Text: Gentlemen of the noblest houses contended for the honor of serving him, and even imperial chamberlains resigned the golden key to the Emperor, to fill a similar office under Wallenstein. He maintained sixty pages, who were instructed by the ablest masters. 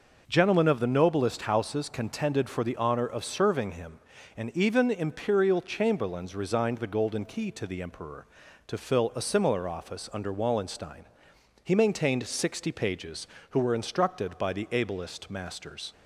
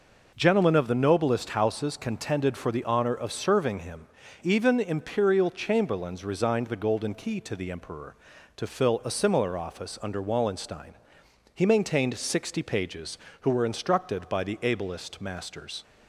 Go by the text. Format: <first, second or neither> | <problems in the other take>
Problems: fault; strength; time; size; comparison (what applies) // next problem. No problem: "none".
first | skips "and"; at 4.2 s